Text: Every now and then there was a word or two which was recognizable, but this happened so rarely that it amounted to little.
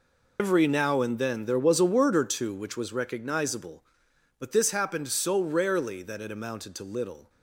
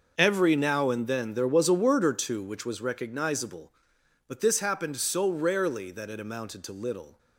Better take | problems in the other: second | loses the start of "Every"; at 0.3 s; 105 ms

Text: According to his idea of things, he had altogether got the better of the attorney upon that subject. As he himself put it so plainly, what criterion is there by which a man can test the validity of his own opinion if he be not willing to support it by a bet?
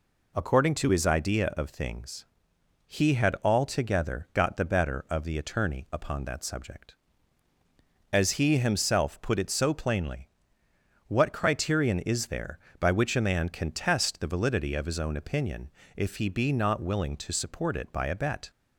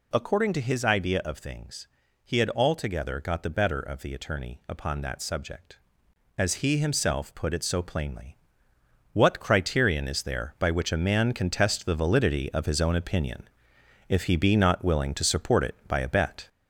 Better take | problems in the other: first | gets louder; noticeable; throughout; 4.5 dB // pauses between "opinion" and "if"; noticeable; at 13.4 s; 0.64 s long; slight in the first

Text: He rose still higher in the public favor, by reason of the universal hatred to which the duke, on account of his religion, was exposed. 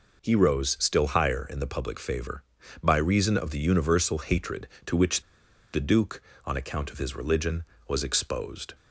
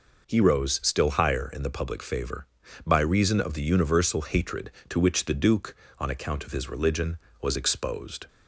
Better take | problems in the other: second | pauses between "which" and "the"; noticeable; at 5.2 s; 0.51 s long

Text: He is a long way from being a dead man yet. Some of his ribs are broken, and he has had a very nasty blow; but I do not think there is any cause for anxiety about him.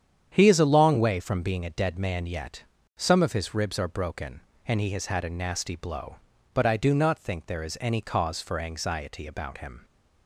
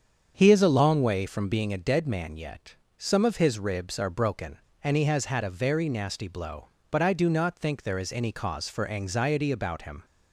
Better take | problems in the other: second | starts louder than the rest; strong; until 1.3 s; 8.5 dB; strong in the second // skips "very"; at 5.2 s

